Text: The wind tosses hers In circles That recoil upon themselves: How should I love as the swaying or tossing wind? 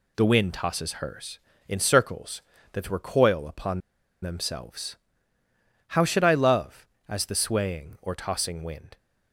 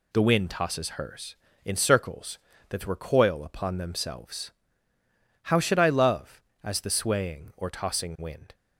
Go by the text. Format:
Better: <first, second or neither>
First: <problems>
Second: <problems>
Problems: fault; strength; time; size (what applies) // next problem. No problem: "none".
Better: second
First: pauses between "upon" and "themselves"; at 3.8 s; 0.41 s long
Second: none